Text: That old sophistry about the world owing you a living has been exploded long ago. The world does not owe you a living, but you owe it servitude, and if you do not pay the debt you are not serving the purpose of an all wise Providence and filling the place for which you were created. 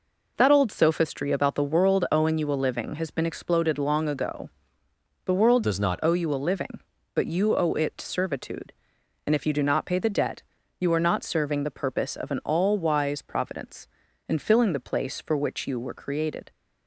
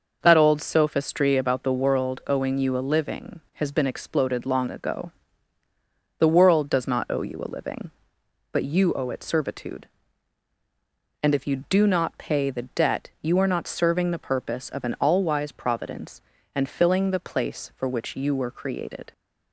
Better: second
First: changes voice from "does" to "not"; from 5.6 to 5.9 s; 0.3 s long // pauses between "debt" and "you"; at 10.4 s; 0.38 s long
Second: none

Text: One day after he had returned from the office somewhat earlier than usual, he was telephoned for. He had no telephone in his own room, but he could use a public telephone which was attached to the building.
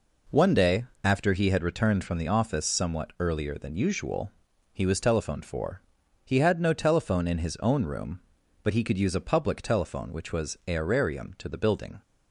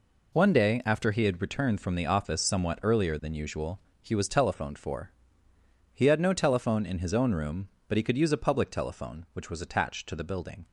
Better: second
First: pauses between "day" and "after"; slight; at 0.8 s; 0.22 s long // says "aerarium" for "attached"; at 10.6 s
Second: none

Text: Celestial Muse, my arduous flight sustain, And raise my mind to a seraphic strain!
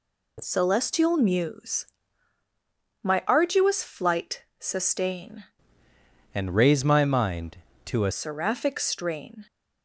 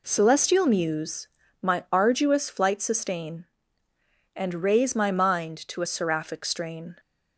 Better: second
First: changes voice from "And" to "a"; from 6.3 to 8.1 s; 1.8 s long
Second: none

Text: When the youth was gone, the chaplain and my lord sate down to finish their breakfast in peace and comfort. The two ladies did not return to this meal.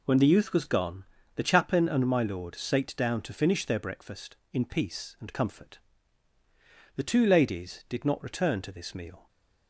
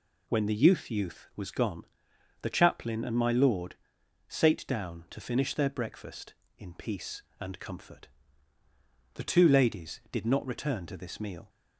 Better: first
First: none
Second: says "youth" twice; at 0.9 s // pauses between "lord" and "sate"; noticeable; at 3.7 s; 0.52 s long

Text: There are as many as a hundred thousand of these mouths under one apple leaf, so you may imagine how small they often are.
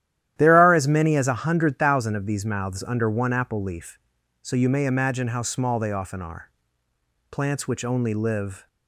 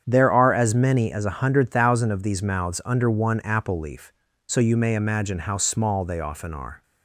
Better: second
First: starts louder than the rest; strong; until 1.3 s; 12 dB // goes on to say "Plants which only live"; from 7.3 s on; 1.3 s long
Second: starts louder than the rest; strong; until 1.0 s; 8 dB

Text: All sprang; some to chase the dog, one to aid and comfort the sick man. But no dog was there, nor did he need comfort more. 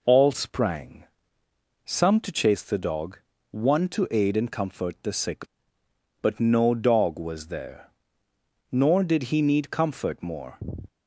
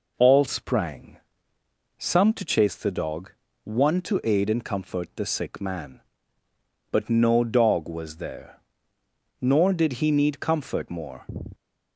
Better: second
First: skips "man"; at 5.8 s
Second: none

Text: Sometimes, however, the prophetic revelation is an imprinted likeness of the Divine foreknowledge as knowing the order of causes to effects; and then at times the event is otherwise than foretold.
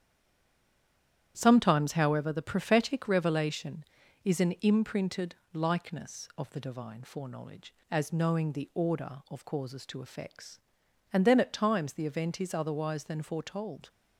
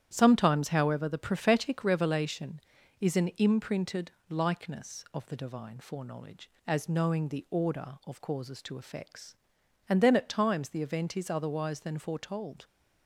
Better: second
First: stays silent before the first word; noticeable; until 1.3 s; 1.3 s long // starts louder than the rest; strong; until 2.3 s; 10.5 dB // pauses between "imprinted" and "likeness"; slight; at 5.3 s; 0.18 s long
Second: starts louder than the rest; strong; until 1.1 s; 10.5 dB // pauses between "imprinted" and "likeness"; slight; at 4.0 s; 0.18 s long

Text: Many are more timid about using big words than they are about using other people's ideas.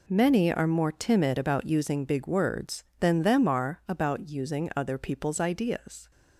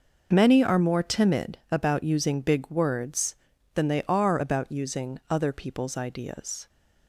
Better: second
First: says "them" for "they"; at 3.2 s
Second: none

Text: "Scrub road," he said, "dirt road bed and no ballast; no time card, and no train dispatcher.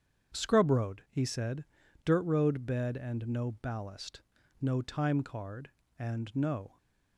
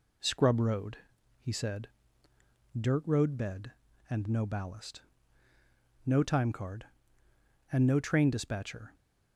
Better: second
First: starts louder than the rest; strong; until 1.4 s; 8 dB // stops before "train dispatcher"; at 6.7 s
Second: none

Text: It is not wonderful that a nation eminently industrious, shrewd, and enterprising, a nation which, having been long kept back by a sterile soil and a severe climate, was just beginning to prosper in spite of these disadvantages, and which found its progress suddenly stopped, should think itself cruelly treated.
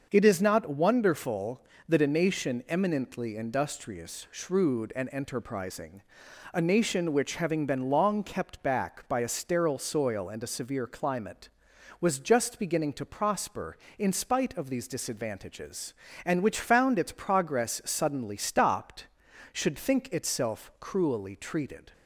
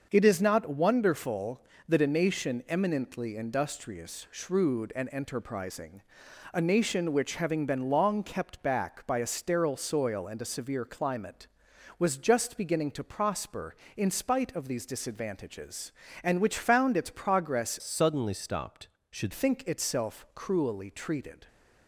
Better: first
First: starts louder than the rest; until 1.1 s; 6.5 dB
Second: starts louder than the rest; until 1.1 s; 6.5 dB // changes voice from "suddenly" to "should"; from 17.8 to 19.3 s; 1.5 s long

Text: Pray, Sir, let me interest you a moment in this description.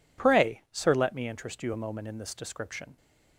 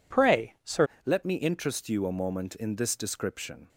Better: first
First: none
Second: changes voice at "let"; from 1.0 s on; 2.6 s long

